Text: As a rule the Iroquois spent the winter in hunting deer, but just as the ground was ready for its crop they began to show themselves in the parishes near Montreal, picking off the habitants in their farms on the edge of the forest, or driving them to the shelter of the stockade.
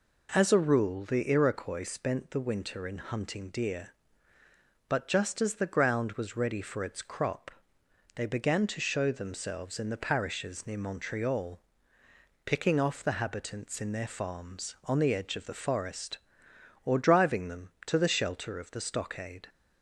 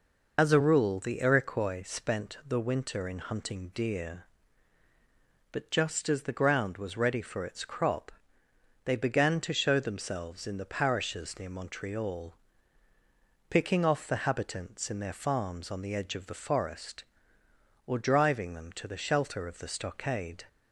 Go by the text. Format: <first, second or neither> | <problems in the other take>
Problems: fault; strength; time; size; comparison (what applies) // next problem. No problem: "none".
first | loses the start of "As"; at 0.3 s; 115 ms // pauses between "crop" and "they"; noticeable; at 8.1 s; 0.72 s long; noticeable in the first